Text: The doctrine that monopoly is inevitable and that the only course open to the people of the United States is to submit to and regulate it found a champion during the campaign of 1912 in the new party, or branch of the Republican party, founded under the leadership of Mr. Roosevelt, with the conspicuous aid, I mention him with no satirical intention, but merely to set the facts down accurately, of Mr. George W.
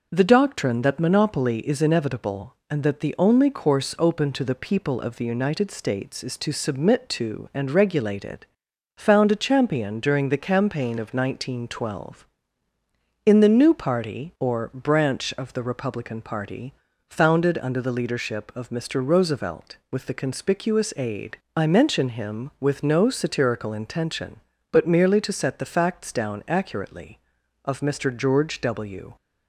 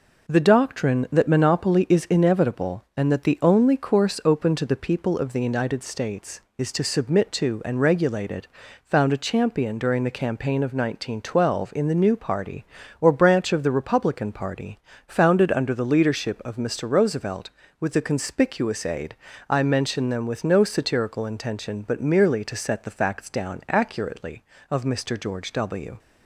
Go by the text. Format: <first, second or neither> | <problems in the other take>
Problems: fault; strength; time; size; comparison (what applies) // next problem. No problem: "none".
first | pauses between "it" and "found"; at 8.4 s; 0.40 s long; noticeable in the first // says "them" for "him"; at 20.0 s